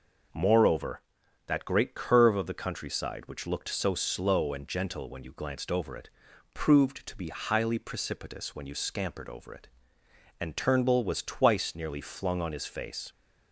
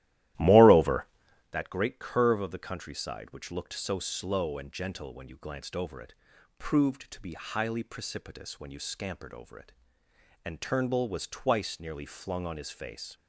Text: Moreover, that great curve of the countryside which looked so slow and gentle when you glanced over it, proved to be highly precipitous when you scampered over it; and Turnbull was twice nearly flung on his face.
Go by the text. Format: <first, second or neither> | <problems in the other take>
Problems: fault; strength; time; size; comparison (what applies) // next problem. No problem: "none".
first | starts louder than the rest; strong; until 1.6 s; 14.5 dB